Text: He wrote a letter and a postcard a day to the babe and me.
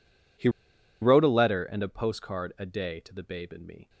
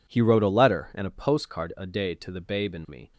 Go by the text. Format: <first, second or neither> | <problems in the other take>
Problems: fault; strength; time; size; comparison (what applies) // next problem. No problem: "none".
second | pauses between "He" and "wrote"; noticeable; at 0.4 s; 0.52 s long